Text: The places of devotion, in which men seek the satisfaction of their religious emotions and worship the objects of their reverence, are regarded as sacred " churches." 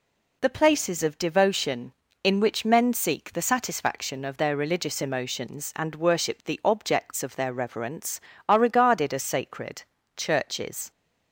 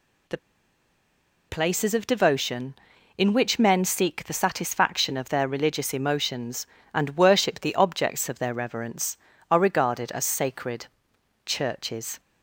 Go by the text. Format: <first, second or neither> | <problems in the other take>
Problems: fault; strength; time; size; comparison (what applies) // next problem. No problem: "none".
first | pauses between "The" and "places"; at 0.3 s; 1.1 s long